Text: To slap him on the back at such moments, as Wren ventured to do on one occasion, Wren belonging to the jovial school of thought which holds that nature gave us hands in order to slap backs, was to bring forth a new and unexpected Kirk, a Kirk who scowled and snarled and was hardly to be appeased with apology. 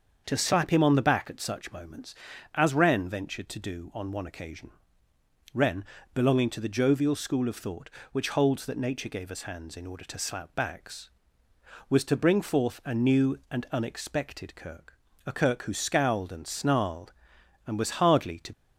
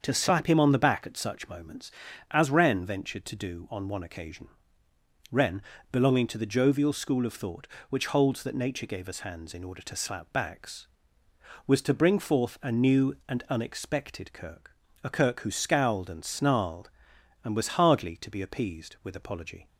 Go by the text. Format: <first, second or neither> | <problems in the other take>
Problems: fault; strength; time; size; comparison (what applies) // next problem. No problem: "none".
second | starts louder than the rest; until 1.2 s; 7 dB; also in the second // pauses between "Wren" and "belonging"; slight; at 5.8 s; 0.30 s long; slight in the second // stops before "be appeased with apology"; at 18.5 s